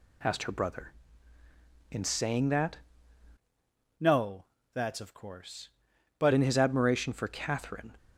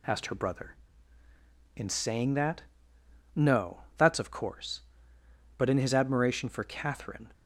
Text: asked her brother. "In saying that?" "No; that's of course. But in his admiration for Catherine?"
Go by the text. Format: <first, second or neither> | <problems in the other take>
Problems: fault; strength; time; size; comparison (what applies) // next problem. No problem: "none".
second | changes voice from "No" to "But"; from 3.9 to 6.3 s; 2.4 s long